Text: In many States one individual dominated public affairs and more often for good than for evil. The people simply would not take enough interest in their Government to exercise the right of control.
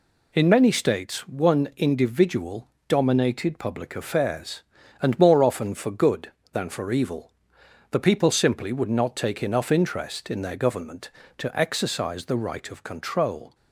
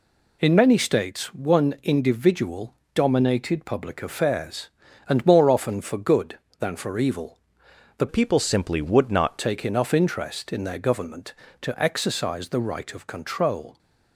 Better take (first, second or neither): first